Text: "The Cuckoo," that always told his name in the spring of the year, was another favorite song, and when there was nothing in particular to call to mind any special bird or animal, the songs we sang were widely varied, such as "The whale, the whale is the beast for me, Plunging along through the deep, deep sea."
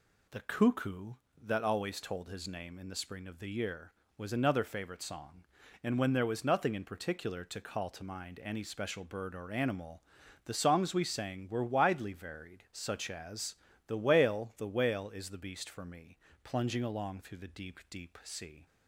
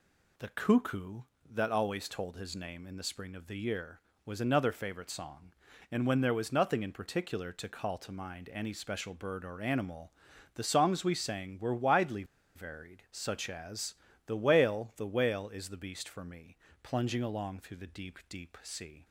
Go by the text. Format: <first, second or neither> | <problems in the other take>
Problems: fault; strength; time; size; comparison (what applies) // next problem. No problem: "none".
first | pauses between "widely" and "varied"; slight; at 12.2 s; 0.31 s long // pauses between "as" and "The"; slight; at 13.9 s; 0.32 s long; slight in the first